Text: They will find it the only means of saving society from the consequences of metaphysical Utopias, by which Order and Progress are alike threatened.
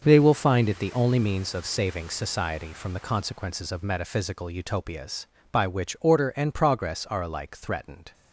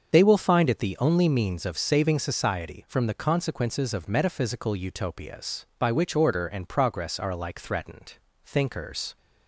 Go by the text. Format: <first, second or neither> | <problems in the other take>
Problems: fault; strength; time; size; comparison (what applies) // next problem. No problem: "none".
first | starts louder than the rest; until 1.1 s; 6.5 dB; noticeable in the first // goes on to say "Thinkers"; noticeable; from 8.4 s on; 0.72 s long